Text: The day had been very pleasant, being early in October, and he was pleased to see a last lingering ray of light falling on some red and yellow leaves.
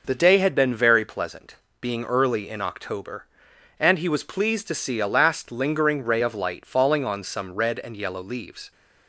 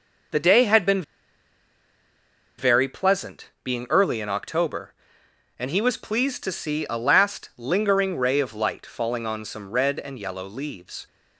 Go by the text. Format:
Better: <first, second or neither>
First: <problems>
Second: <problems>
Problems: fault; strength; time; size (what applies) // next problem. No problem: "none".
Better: first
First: none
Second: pauses between "been" and "very"; strong; at 1.0 s; 1.5 s long